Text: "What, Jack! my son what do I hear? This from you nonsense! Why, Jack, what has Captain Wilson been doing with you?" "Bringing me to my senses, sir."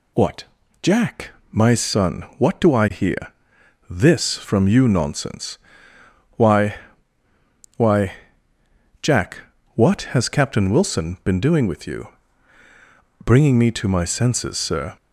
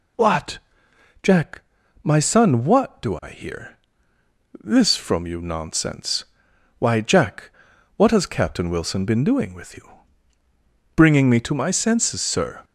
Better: second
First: says "Why" twice; at 7.7 s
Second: none

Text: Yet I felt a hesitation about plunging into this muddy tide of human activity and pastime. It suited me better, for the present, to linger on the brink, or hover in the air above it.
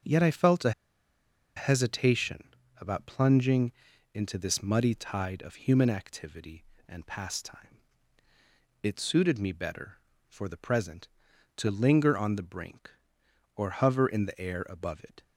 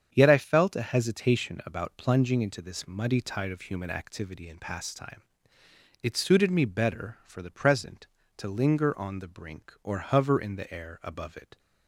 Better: second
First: starts louder than the rest; until 1.9 s; 7 dB // pauses between "a" and "hesitation"; noticeable; at 0.7 s; 0.85 s long // pauses between "hesitation" and "about"; slight; at 2.4 s; 0.30 s long // pauses between "plunging" and "into"; at 3.7 s; 0.42 s long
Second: starts louder than the rest; strong; until 1.1 s; 8 dB

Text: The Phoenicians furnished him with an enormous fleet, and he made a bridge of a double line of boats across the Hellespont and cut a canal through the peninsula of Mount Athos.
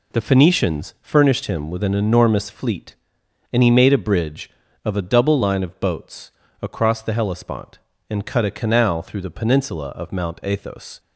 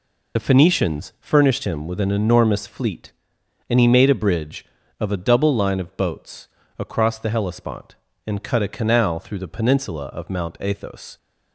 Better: first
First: pauses between "boats" and "across"; slight; at 6.3 s; 0.28 s long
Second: loses the start of "The"; at 0.3 s; 50 ms // pauses between "boats" and "across"; slight; at 6.4 s; 0.28 s long

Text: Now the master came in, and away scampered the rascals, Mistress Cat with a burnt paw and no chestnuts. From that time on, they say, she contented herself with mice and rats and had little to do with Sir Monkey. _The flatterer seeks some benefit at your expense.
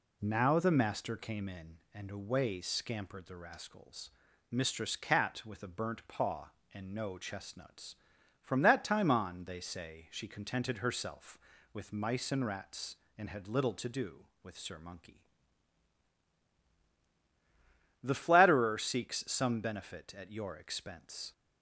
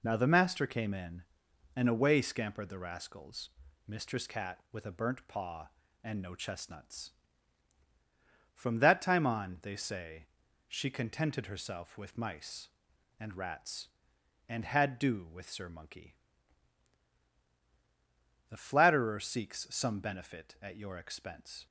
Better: first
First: none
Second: skips "little to"; at 14.9 s

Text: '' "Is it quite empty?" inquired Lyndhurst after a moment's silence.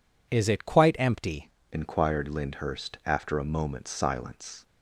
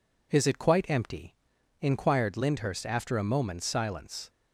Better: second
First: changes voice at "inquired"; from 1.7 s on; 2.9 s long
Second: none

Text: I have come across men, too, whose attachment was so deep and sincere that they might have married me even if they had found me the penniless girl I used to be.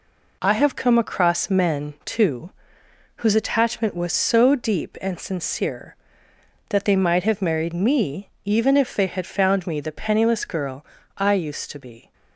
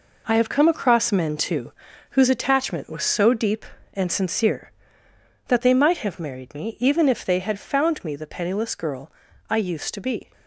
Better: first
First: pauses between "girl" and "I"; slight; at 10.8 s; 0.32 s long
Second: gets quieter; strong; throughout; 8.5 dB // pauses between "girl" and "I"; slight; at 9.1 s; 0.36 s long

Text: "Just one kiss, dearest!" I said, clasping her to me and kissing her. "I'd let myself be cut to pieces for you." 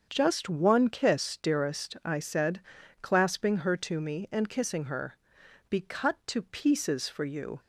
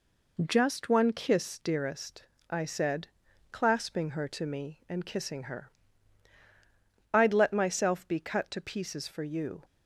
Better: second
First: starts louder than the rest; until 1.1 s; 7 dB // skips "I'd let myself"; at 5.4 s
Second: none

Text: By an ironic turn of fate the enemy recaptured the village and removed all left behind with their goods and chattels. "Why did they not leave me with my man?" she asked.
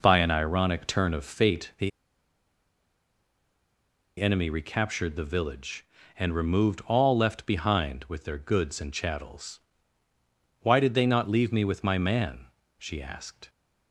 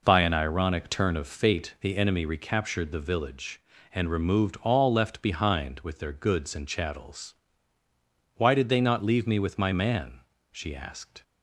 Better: second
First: pauses between "the" and "enemy"; strong; at 1.9 s; 2.2 s long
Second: none

